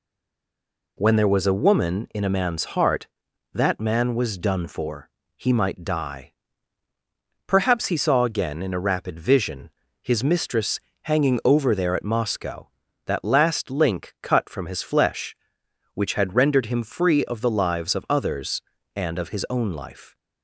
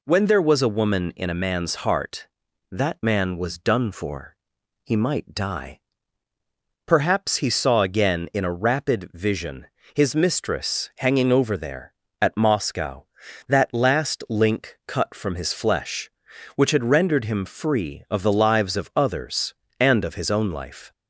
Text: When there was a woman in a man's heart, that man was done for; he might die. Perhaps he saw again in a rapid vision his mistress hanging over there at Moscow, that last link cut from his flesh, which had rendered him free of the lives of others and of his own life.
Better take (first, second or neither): second